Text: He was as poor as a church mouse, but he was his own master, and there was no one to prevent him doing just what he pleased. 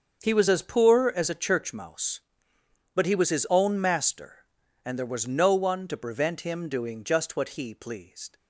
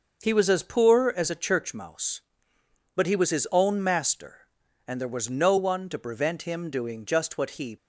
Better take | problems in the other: first | starts louder than the rest; until 1.2 s; 6 dB; also in the first // stops before "pleased"; at 7.7 s

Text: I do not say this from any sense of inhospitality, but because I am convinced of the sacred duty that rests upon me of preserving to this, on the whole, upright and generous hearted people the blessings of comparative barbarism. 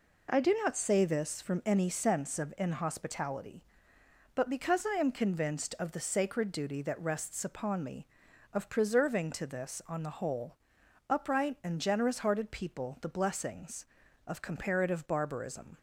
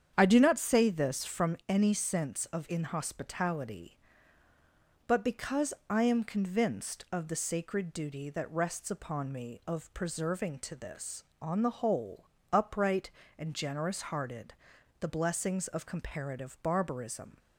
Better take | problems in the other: first | starts louder than the rest; strong; until 1.1 s; 8 dB // pauses between "because" and "I"; slight; at 5.7 s; 0.16 s long // skips "people"; at 14.7 s

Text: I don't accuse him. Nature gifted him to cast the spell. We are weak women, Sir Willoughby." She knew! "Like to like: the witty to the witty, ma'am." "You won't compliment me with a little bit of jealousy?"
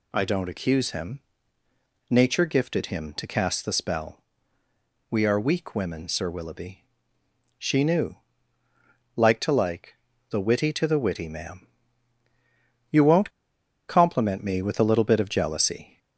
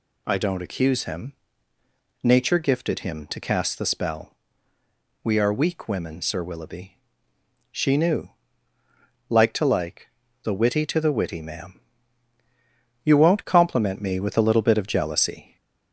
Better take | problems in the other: second | pauses between "won't" and "compliment"; noticeable; at 13.3 s; 0.57 s long

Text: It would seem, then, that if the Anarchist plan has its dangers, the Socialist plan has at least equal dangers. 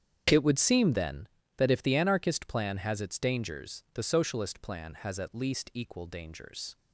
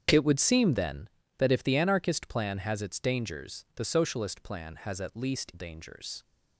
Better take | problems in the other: first | starts louder than the rest; strong; until 1.4 s; 7.5 dB; strong in the first // skips "equal"; at 5.5 s

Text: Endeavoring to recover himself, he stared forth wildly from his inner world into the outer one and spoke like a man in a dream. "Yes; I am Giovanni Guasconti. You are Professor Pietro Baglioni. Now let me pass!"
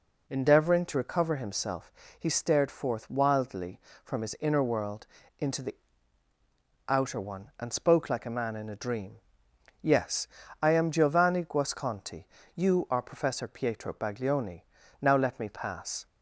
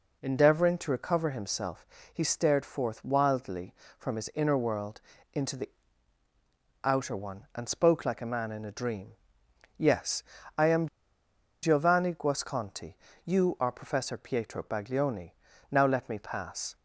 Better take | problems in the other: first | pauses between "world" and "into"; slight; at 4.9 s; 0.34 s long; slight in the first // pauses between "the" and "outer"; at 5.6 s; 1.1 s long; also in the first // pauses between "am" and "Giovanni"; noticeable; at 10.8 s; 0.75 s long

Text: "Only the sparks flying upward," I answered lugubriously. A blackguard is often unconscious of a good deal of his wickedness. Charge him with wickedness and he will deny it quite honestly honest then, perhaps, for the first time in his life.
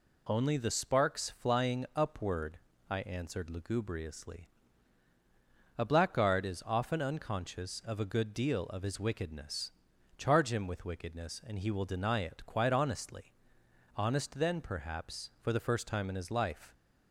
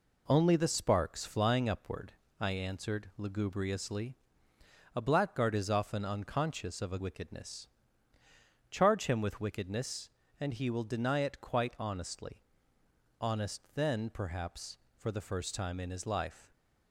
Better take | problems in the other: first | skips "good deal of his"; at 6.9 s // pauses between "honestly" and "honest"; noticeable; at 12.3 s; 0.84 s long; noticeable in the first

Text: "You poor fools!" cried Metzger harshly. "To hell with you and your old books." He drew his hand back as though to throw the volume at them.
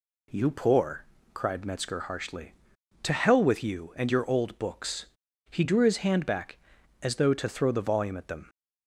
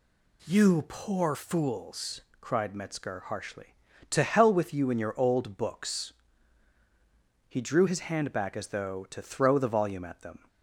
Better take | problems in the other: second | skips "fools"; at 1.1 s

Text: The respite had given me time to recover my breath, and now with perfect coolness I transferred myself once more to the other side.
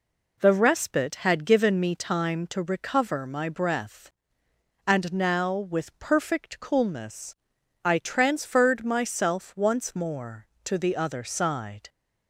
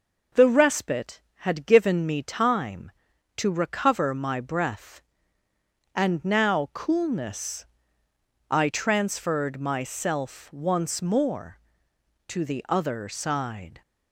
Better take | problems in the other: first | skips "with perfect"; at 6.7 s // pauses between "coolness" and "I"; noticeable; at 7.6 s; 0.82 s long; noticeable in the first

